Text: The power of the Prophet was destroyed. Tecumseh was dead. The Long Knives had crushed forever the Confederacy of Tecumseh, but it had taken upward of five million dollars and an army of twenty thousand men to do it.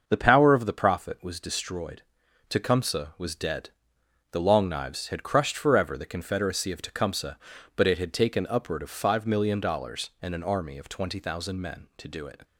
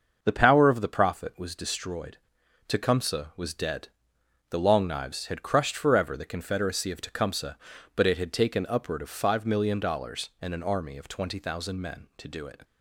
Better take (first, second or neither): neither